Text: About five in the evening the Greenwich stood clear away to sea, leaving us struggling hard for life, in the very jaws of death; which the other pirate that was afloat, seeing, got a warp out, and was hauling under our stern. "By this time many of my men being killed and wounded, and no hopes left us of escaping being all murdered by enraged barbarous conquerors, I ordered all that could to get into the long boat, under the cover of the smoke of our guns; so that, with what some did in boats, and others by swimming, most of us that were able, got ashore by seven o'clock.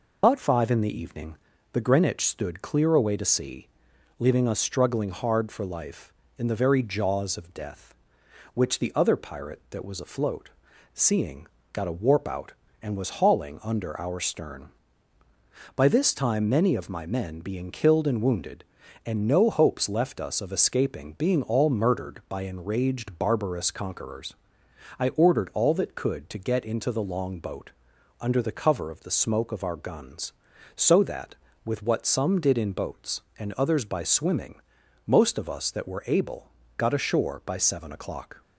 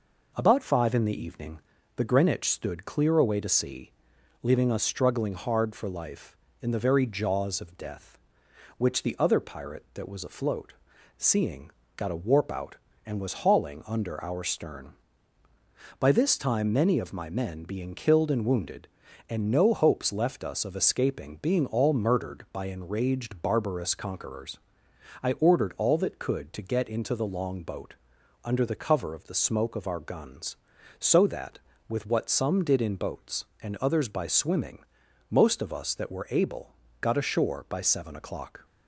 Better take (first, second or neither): second